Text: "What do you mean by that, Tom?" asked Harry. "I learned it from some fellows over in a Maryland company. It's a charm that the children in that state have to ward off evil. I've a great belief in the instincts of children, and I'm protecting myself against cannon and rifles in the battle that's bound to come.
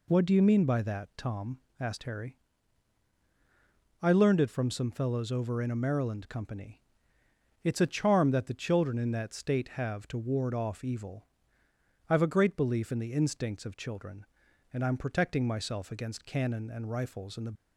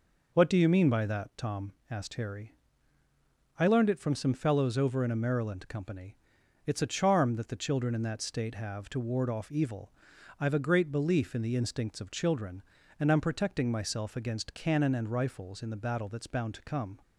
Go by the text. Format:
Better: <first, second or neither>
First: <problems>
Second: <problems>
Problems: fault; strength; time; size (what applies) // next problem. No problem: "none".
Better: second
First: stops before "battle that's bound to come"; at 17.5 s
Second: none